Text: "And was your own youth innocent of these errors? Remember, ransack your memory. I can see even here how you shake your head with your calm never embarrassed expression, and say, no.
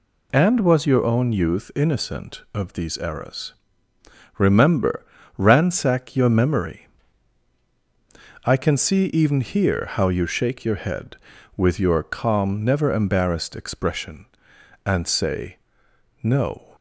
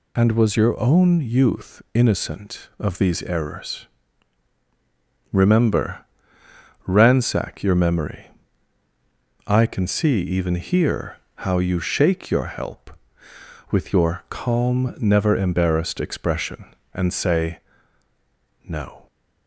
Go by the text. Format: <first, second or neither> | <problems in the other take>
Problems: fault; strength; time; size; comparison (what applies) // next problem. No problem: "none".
first | pauses between "here" and "how"; slight; at 11.1 s; 0.20 s long // says "help" for "head"; at 12.4 s